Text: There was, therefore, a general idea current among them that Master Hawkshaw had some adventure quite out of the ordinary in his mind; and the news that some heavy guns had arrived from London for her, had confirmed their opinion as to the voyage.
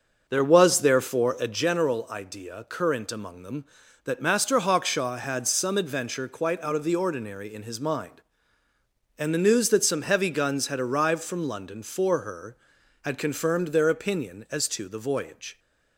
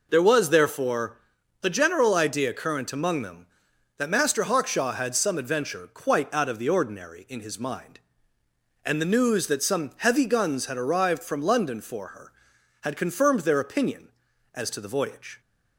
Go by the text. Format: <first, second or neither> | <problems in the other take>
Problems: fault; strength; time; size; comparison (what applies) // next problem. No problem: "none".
second | starts louder than the rest; until 1.7 s; 6.5 dB